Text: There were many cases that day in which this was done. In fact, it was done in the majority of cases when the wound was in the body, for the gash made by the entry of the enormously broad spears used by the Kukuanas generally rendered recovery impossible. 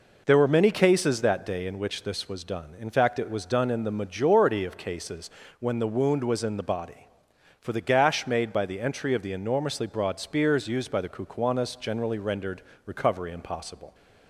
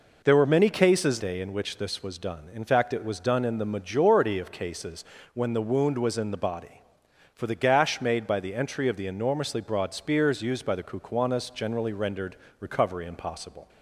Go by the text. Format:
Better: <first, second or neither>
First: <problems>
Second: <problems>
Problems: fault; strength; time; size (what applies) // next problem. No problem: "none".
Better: first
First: pauses between "cases" and "when"; slight; at 5.2 s; 0.30 s long // pauses between "rendered" and "recovery"; slight; at 12.6 s; 0.24 s long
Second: skips "that"; at 1.1 s // pauses between "cases" and "when"; slight; at 5.0 s; 0.30 s long // pauses between "rendered" and "recovery"; slight; at 12.3 s; 0.24 s long